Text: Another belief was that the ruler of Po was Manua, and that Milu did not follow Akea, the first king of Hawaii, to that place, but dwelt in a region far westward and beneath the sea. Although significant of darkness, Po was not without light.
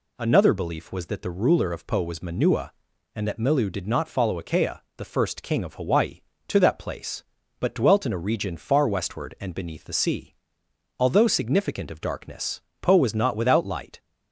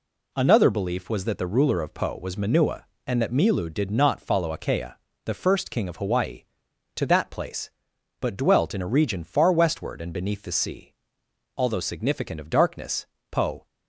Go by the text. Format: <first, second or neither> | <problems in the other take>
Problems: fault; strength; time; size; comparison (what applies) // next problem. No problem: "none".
first | stops before "was not without light"; at 13.6 s